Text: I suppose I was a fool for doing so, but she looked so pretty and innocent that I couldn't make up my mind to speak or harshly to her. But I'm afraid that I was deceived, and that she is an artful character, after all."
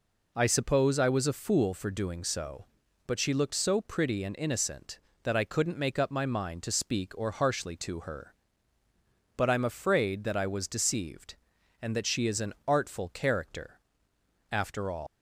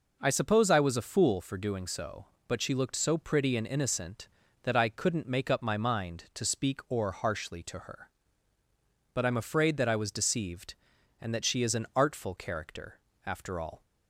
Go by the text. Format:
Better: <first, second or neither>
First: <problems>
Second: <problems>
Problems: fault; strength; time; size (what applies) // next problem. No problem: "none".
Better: second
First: leaves "all" unfinished; at 15.0 s; 120 ms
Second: none